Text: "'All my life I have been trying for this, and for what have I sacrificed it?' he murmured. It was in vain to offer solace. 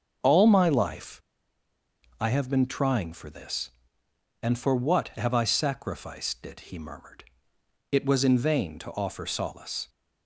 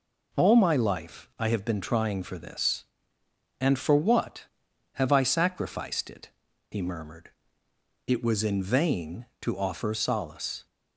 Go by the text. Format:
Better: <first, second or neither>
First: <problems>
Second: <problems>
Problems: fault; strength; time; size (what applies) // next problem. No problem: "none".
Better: second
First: starts louder than the rest; until 2.2 s; 7 dB // pauses between "life" and "I"; at 1.1 s; 1.0 s long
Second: none